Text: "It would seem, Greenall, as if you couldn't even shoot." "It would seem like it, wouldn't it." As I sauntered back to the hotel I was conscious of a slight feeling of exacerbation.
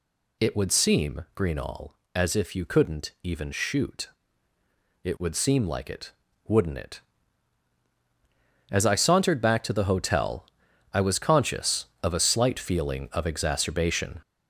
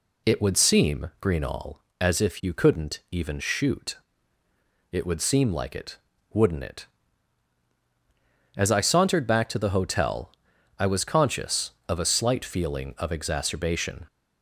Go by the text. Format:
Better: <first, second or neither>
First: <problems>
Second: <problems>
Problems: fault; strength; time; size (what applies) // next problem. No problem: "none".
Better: second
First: gets louder; noticeable; throughout; 5.5 dB // pauses between "hotel" and "I"; noticeable; at 10.4 s; 0.48 s long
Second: pauses between "hotel" and "I"; noticeable; at 10.3 s; 0.48 s long